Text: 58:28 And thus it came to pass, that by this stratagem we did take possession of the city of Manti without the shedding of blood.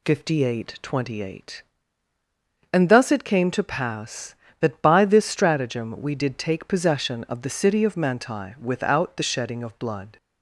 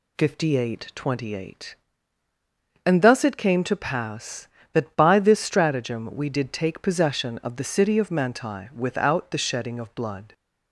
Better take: neither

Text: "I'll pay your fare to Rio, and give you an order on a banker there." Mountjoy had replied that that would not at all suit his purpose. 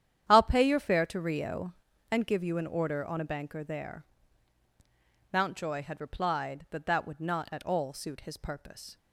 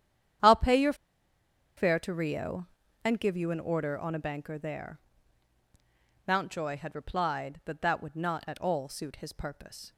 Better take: first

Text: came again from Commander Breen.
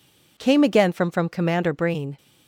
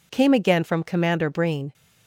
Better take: second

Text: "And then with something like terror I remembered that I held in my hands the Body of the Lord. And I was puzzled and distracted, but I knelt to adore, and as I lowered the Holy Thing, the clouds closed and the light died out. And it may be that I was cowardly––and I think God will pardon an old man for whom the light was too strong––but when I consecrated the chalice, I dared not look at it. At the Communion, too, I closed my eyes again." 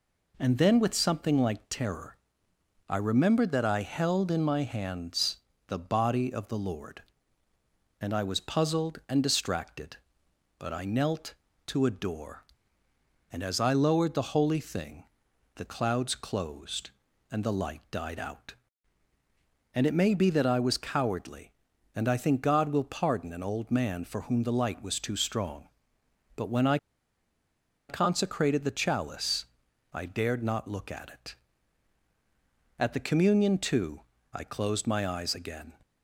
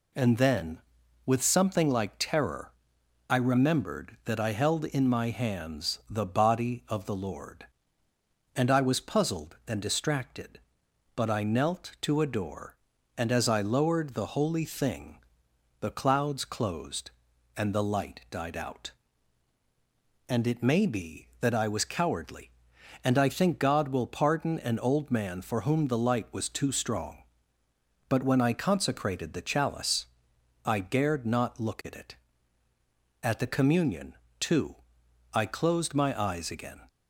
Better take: second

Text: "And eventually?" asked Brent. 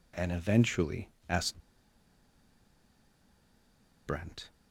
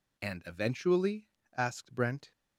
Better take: second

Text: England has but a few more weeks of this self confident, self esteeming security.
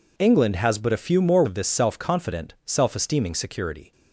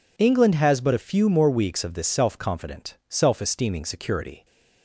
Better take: second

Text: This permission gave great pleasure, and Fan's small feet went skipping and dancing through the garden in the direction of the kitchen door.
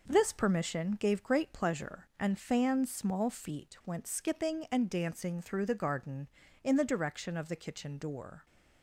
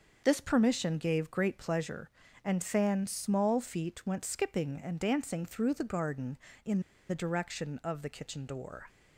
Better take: first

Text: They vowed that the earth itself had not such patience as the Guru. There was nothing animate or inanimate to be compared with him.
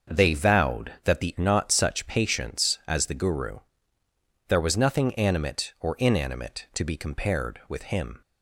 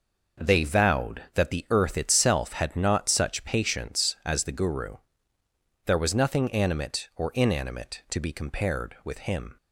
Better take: second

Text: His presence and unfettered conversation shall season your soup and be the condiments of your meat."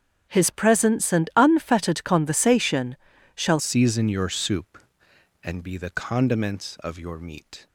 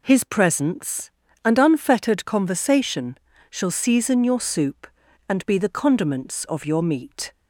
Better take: second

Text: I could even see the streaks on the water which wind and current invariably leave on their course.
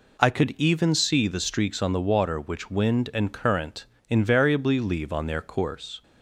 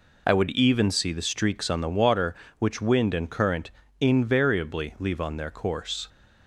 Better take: first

